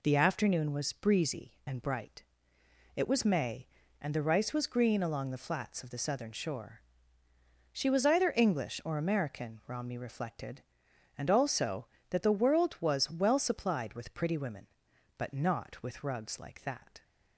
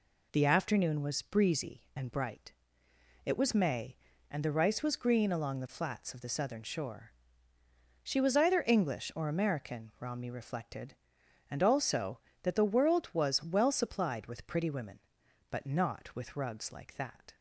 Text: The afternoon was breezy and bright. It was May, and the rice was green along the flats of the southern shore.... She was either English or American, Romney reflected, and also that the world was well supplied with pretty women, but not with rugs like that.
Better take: neither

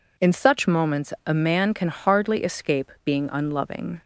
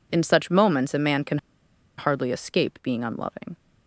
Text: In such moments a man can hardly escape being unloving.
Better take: first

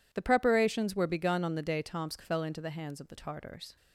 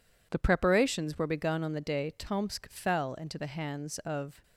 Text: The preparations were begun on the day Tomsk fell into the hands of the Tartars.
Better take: first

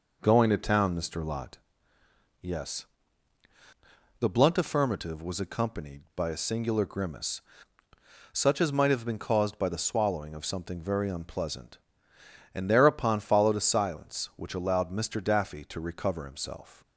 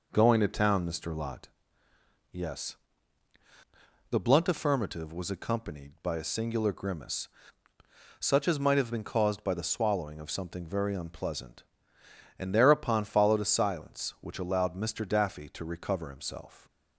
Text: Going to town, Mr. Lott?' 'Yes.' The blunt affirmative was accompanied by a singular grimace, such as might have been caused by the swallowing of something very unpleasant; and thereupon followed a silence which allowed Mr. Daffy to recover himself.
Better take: neither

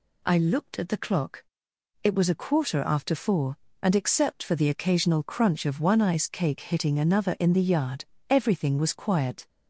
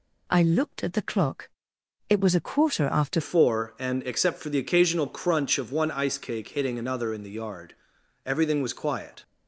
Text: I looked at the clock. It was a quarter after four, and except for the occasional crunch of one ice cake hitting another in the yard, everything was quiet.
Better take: first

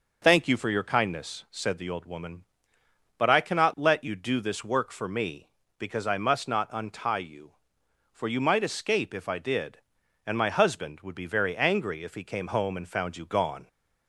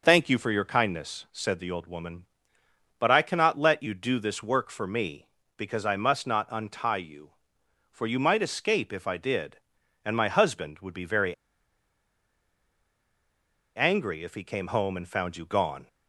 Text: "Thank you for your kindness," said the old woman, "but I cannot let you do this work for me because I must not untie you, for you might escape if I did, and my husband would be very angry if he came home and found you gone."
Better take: first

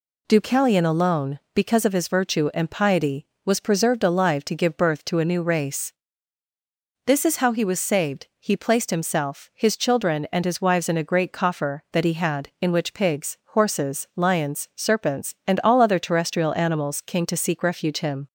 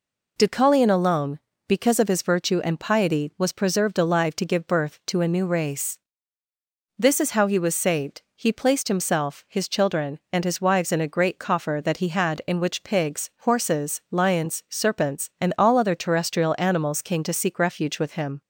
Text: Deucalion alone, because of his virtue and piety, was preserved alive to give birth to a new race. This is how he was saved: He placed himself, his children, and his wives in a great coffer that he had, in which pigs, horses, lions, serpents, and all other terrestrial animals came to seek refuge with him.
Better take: second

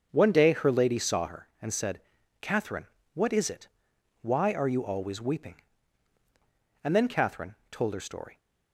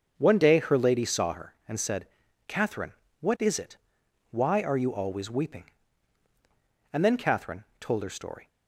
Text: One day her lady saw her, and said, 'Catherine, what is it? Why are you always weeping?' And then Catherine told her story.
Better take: neither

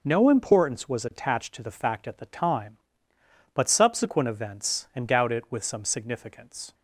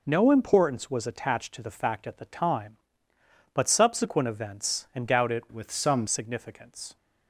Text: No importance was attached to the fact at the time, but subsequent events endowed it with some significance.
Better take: first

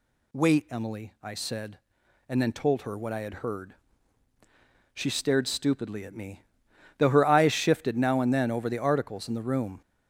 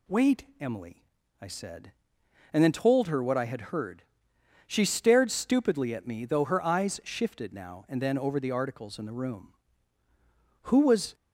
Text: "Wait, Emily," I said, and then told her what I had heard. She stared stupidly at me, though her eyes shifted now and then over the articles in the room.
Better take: first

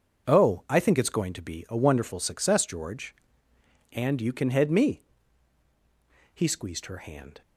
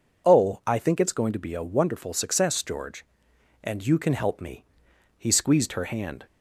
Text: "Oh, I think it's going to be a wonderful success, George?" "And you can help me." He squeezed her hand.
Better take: second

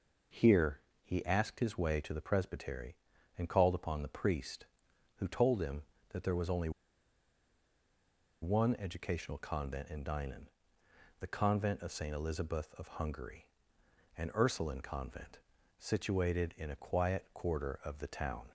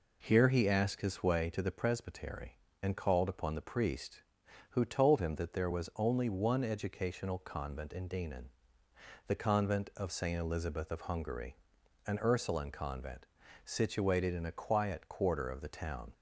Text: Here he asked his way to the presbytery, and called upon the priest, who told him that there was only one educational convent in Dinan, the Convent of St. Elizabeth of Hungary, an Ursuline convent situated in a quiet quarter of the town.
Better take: second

